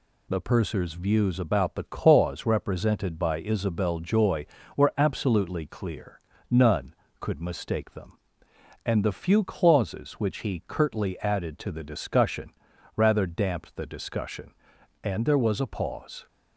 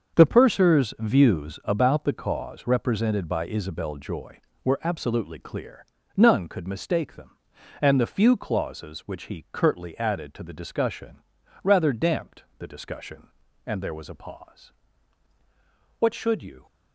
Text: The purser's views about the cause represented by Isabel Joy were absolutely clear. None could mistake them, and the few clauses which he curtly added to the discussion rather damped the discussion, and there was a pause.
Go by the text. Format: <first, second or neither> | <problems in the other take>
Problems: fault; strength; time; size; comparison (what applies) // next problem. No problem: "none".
first | starts louder than the rest; until 1.2 s; 6.5 dB // pauses between "discussion" and "rather"; noticeable; at 11.1 s; 0.46 s long; noticeable in the first // pauses between "damped" and "the"; slight; at 12.4 s; 0.16 s long // goes on to say "What should you"; noticeable; from 15.9 s on; 0.68 s long